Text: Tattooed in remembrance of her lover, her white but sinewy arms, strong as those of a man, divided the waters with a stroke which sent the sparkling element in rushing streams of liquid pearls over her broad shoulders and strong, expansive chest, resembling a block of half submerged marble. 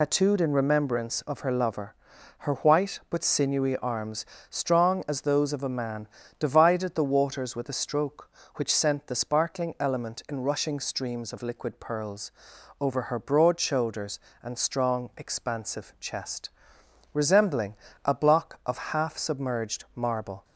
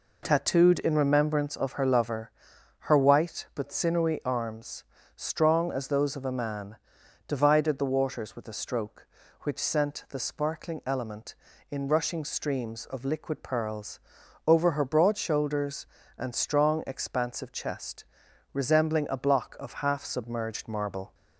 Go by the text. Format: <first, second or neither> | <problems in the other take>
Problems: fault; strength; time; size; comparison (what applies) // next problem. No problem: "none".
second | loses the start of "Tattooed"; at 0.0 s; 105 ms // pauses between "pearls" and "over"; noticeable; at 12.3 s; 0.48 s long; noticeable in the second // pauses between "resembling" and "a"; slight; at 17.7 s; 0.30 s long